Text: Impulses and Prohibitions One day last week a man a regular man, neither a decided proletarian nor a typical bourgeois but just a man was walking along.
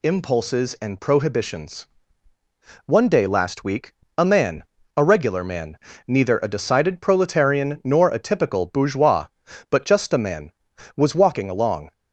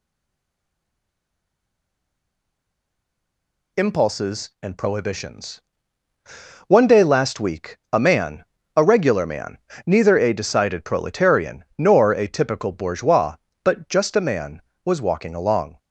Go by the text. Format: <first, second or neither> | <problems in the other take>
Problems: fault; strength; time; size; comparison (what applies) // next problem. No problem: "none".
first | stays silent before the first word; strong; until 3.7 s; 3.7 s long // pauses between "Prohibitions" and "One"; at 5.5 s; 1.0 s long; also in the first // pauses between "week" and "a"; slight; at 7.7 s; 0.16 s long; slight in the first // pauses between "man" and "a"; slight; at 8.4 s; 0.32 s long; slight in the first